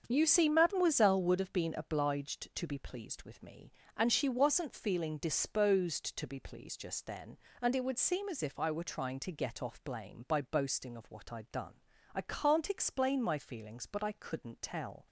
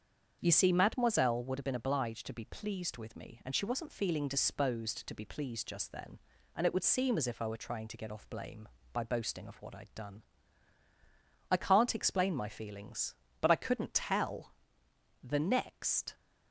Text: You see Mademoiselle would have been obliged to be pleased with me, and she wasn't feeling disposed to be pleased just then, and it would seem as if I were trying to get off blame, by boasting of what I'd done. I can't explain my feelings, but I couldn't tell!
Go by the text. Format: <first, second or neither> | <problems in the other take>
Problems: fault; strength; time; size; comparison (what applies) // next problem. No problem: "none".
first | starts louder than the rest; strong; until 1.4 s; 7.5 dB; also in the first // goes on to say "The next"; noticeable; from 15.2 s on; 0.92 s long